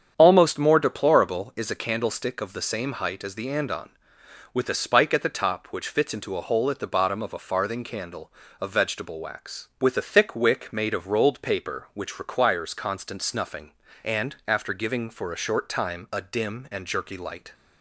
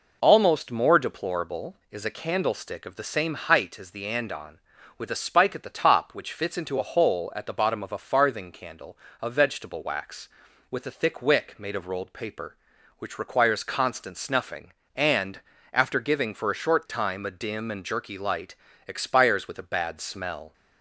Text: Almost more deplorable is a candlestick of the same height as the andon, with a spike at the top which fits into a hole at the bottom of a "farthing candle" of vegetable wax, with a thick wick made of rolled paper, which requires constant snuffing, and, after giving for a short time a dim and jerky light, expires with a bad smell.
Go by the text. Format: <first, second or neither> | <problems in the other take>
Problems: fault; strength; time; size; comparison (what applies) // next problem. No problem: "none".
second | starts louder than the rest; strong; until 1.1 s; 8 dB // stops before "expires with a bad smell"; at 17.5 s